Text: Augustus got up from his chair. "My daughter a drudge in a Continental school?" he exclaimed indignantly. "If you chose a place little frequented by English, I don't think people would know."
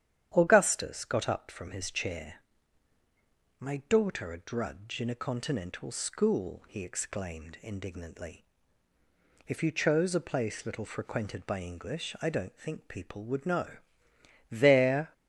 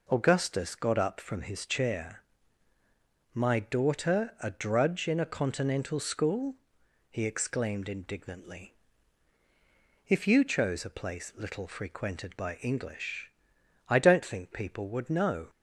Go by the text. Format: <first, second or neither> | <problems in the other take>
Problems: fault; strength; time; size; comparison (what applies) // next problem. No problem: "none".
second | starts louder than the rest; strong; until 1.3 s; 10 dB // goes on to say "There"; noticeable; from 14.5 s on; 0.62 s long